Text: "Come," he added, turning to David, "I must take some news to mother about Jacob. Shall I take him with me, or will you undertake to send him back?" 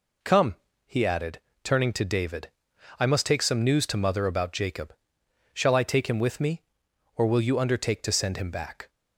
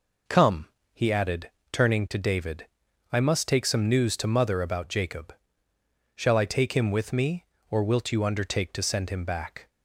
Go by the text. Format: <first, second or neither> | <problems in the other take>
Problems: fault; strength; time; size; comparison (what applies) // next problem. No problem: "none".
first | says "wilt" for "will"; at 7.8 s